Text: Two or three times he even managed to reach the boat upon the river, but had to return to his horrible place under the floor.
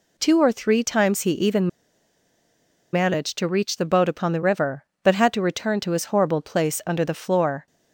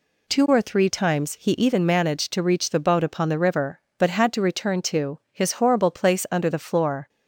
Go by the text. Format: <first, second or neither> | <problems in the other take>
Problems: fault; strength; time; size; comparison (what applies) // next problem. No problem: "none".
second | pauses between "even" and "managed"; at 1.6 s; 1.2 s long